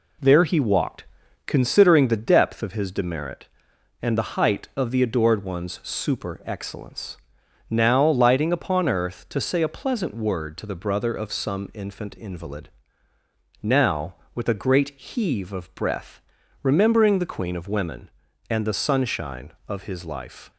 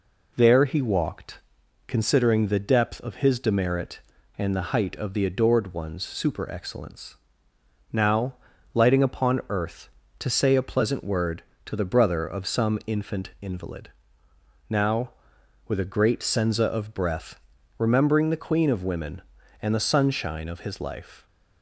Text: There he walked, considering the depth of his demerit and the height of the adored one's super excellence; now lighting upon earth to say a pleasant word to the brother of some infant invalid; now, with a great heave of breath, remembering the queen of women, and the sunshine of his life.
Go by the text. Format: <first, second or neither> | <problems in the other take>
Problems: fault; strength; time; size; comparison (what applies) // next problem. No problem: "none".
first | pauses between "now" and "lighting"; at 8.3 s; 0.40 s long // says "senza" for "heave"; at 16.2 s